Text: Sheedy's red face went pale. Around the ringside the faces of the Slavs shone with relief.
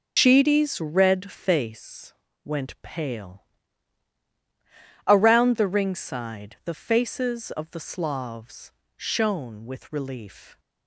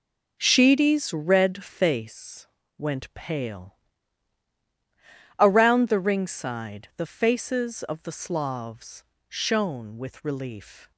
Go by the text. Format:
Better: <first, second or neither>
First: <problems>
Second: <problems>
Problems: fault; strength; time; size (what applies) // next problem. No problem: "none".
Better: second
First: loses the start of "Sheedy's"; at 0.1 s; 100 ms // pauses between "face" and "went"; slight; at 2.1 s; 0.32 s long // pauses between "Slavs" and "shone"; slight; at 8.7 s; 0.28 s long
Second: pauses between "face" and "went"; slight; at 2.4 s; 0.32 s long // pauses between "Slavs" and "shone"; slight; at 9.0 s; 0.28 s long